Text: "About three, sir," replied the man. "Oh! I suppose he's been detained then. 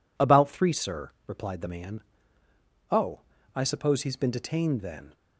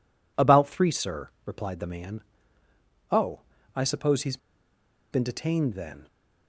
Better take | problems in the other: first | pauses between "he's" and "been"; noticeable; at 4.3 s; 0.75 s long

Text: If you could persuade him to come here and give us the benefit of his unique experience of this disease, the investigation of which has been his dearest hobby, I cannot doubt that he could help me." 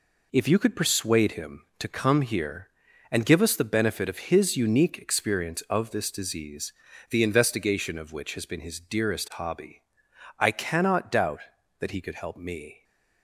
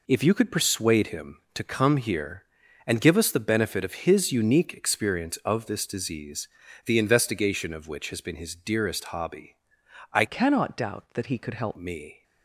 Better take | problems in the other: first | changes voice from "cannot" to "help"; from 10.2 to 11.7 s; 1.5 s long

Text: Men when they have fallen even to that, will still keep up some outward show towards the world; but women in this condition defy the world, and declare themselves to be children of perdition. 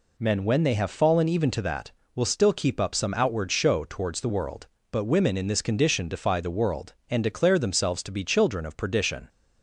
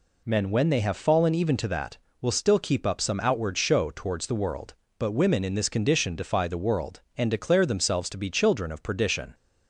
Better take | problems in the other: neither | none

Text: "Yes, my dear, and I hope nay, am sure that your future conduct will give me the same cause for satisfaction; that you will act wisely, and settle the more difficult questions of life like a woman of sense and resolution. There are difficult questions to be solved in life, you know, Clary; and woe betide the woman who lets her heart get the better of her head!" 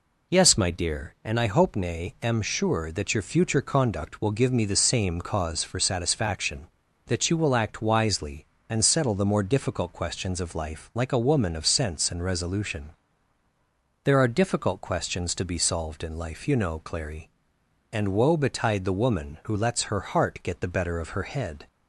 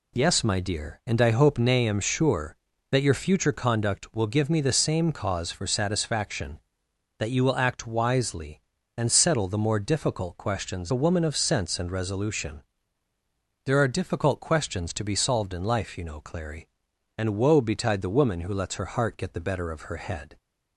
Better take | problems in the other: first | skips "of life like"; at 10.9 s

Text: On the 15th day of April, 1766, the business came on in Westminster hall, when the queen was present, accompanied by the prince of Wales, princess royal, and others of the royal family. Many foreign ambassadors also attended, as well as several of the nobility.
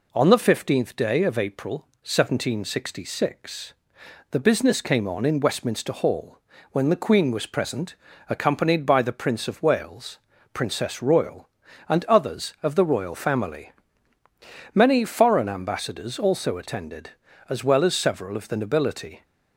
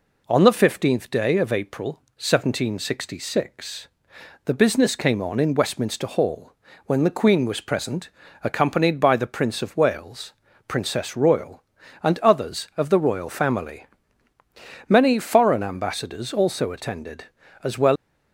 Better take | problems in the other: first | stops before "as several of the nobility"; at 17.9 s

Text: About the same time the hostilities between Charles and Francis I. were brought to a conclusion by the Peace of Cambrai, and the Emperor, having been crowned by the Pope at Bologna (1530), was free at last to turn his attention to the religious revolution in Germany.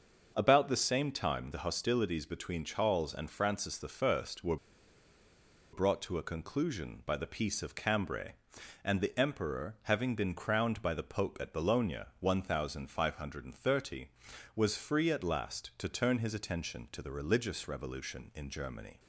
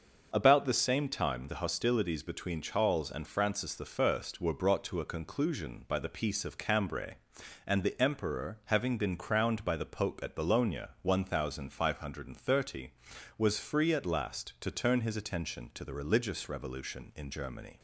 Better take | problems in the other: second | starts louder than the rest; until 1.3 s; 6 dB; also in the second // pauses between "were" and "brought"; at 4.5 s; 1.1 s long

